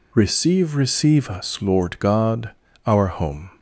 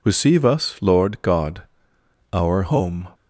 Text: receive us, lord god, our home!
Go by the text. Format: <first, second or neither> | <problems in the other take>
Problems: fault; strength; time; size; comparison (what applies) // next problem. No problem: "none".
second | says "receive" twice; at 0.7 s